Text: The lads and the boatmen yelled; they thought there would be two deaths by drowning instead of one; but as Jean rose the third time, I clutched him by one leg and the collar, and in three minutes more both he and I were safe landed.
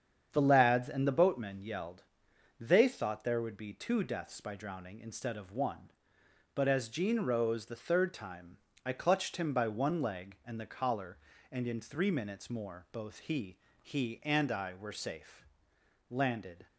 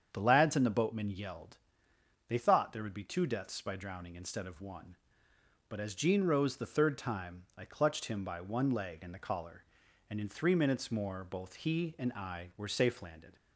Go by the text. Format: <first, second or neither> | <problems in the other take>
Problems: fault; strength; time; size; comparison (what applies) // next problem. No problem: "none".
second | starts louder than the rest; strong; until 1.3 s; 8 dB; strong in the second // says "he" twice; at 13.8 s // pauses between "safe" and "landed"; noticeable; at 15.4 s; 0.66 s long